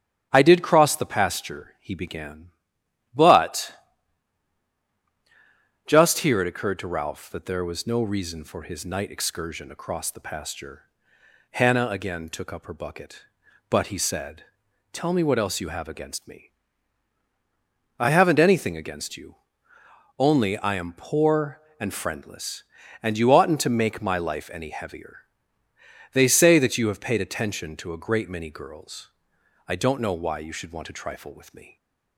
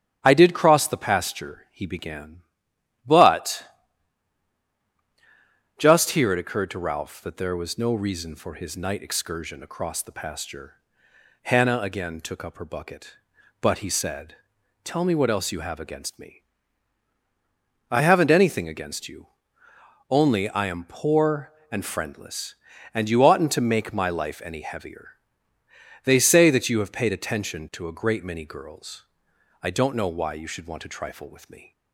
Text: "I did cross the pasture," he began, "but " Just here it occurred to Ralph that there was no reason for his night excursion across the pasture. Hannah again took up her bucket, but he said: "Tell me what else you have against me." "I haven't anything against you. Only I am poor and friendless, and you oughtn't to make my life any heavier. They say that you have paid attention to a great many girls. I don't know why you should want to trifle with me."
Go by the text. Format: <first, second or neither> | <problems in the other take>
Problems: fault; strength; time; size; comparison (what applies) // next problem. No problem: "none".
neither | starts louder than the rest; strong; the same in both